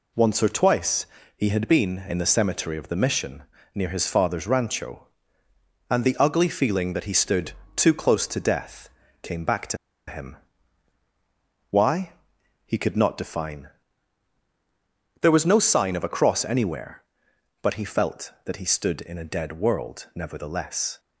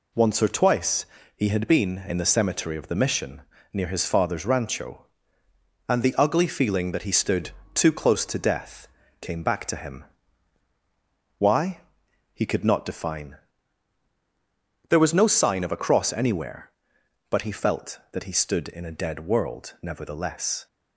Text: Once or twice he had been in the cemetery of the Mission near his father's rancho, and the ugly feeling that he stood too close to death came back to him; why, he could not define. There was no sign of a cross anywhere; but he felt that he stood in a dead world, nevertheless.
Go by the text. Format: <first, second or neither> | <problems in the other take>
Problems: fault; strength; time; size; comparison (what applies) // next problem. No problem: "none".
second | pauses between "twice" and "he"; slight; at 1.0 s; 0.28 s long; slight in the second // pauses between "Mission" and "near"; slight; at 3.4 s; 0.30 s long; slight in the second // pauses between "stood" and "too"; slight; at 7.5 s; 0.22 s long; slight in the second // pauses between "death" and "came"; slight; at 8.8 s; 0.34 s long; slight in the second // pauses between "to" and "him"; slight; at 9.7 s; 0.32 s long